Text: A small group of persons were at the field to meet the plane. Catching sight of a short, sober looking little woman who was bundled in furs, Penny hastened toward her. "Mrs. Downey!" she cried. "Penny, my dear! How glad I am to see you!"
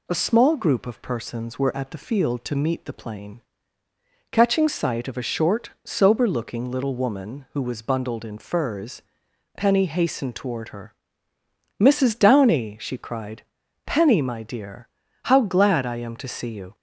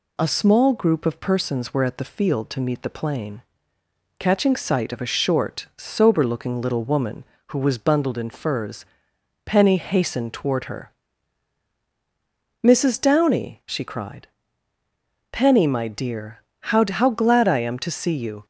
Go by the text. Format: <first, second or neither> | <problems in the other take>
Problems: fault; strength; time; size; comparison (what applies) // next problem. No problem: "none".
first | says "How" twice; at 16.8 s